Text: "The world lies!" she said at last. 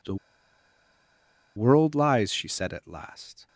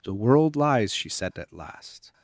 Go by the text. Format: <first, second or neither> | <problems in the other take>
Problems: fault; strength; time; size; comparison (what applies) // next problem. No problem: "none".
second | pauses between "The" and "world"; strong; at 0.1 s; 1.4 s long